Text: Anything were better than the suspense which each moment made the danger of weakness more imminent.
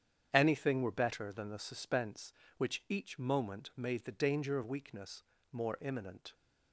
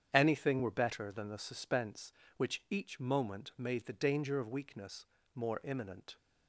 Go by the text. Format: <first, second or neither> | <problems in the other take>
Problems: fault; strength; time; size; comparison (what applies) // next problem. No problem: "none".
neither | starts louder than the rest; strong; the same in both // pauses between "weakness" and "more"; slight; the same in both